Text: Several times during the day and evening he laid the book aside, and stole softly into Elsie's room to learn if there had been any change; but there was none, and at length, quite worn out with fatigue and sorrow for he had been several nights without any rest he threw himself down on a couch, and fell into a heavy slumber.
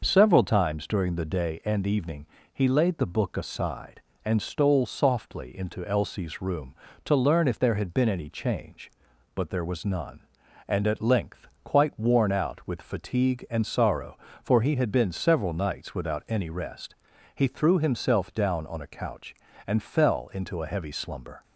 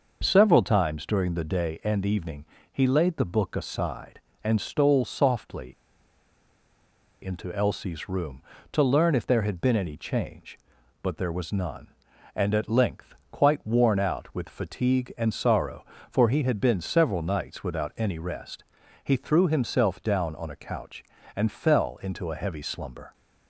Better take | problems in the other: first | starts louder than the rest; noticeable; until 1.2 s; 6 dB; noticeable in the first // pauses between "evening" and "he"; slight; at 2.4 s; 0.28 s long; slight in the first // pauses between "softly" and "into"; strong; at 5.7 s; 1.5 s long // pauses between "rest" and "he"; at 18.6 s; 0.40 s long; also in the first

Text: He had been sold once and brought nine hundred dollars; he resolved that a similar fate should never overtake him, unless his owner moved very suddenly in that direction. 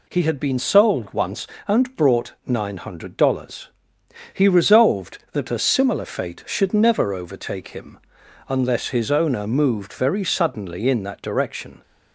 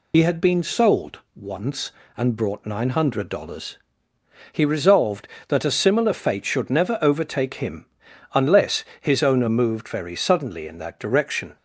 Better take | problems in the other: first | loses the start of "He"; at 0.1 s; 65 ms // pauses between "sold" and "once"; slight; at 1.2 s; 0.16 s long // pauses between "unless" and "his"; slight; at 8.8 s; 0.16 s long

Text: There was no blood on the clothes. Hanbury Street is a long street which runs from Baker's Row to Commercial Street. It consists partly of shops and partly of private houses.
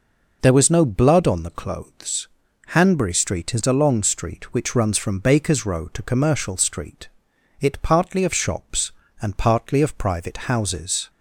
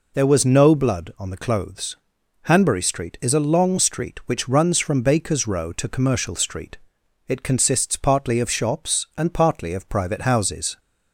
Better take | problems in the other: second | skips "consists"; at 7.8 s

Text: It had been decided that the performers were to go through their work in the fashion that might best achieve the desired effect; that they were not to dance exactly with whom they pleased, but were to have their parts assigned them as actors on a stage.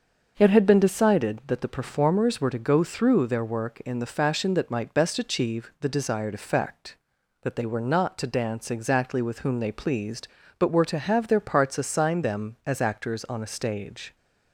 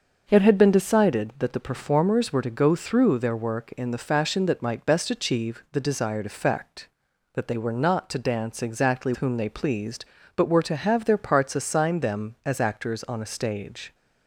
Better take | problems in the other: first | starts louder than the rest; until 1.2 s; 6 dB; also in the first // skips "with"; at 9.1 s

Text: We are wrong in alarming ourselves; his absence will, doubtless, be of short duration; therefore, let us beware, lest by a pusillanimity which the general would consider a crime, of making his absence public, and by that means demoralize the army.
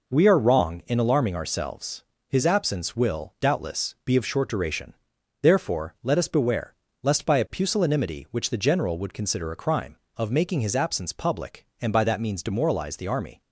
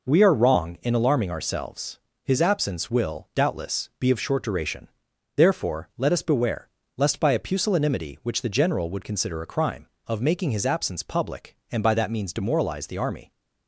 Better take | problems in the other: neither | none

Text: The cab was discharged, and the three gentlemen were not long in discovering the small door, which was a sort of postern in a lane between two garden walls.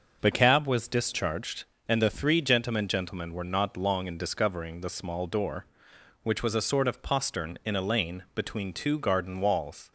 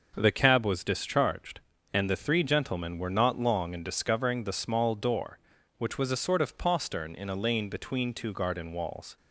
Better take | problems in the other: second | says "gentlemen" twice; at 2.8 s

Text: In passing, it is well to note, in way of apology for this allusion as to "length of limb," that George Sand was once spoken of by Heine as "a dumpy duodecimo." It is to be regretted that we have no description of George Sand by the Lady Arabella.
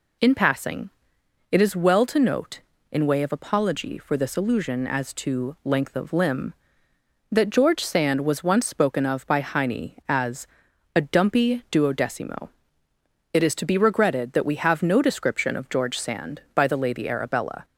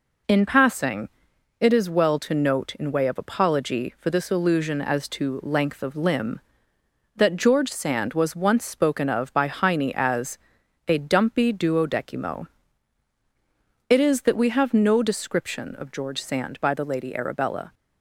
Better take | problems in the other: first | pauses between "as" and "a"; noticeable; at 10.3 s; 0.50 s long; noticeable in the first // skips "to be regretted"; at 14.2 s

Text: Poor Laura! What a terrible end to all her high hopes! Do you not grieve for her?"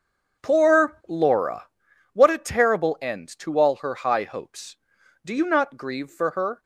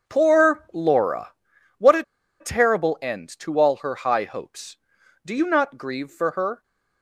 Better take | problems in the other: first | starts louder than the rest; until 1.1 s; 6.5 dB; also in the first // pauses between "a" and "terrible"; at 2.0 s; 0.37 s long

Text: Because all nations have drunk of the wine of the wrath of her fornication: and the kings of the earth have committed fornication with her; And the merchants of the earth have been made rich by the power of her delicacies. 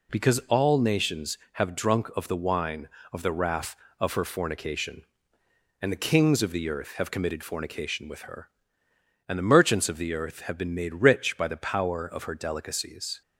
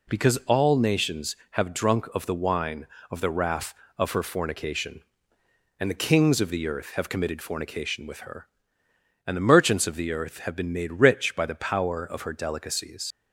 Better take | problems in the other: first | leaves "delicacies" unfinished; at 13.1 s; 90 ms

